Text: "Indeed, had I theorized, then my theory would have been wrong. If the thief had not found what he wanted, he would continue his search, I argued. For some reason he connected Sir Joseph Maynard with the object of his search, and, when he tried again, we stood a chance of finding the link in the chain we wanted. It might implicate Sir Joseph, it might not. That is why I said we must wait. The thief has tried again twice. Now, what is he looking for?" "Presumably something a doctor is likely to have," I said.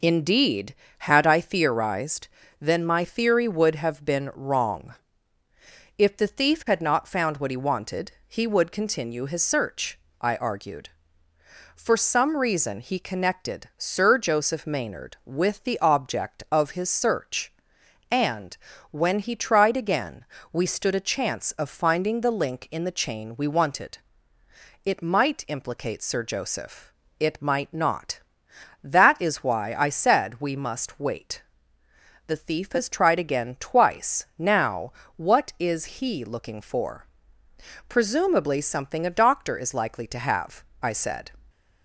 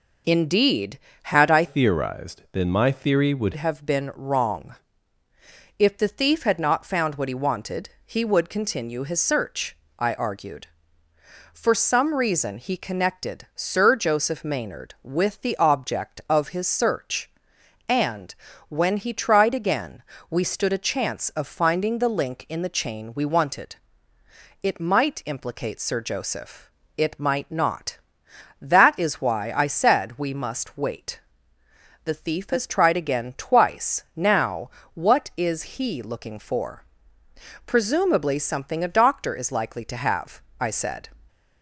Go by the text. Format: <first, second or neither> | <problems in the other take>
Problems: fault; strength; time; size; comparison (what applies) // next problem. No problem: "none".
first | changes voice from "theorized" to "would"; from 1.6 to 3.5 s; 1.9 s long